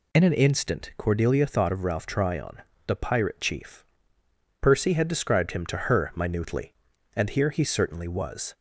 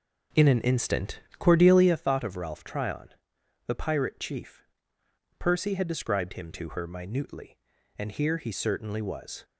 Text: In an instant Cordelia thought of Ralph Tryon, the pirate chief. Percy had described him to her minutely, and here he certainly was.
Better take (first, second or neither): first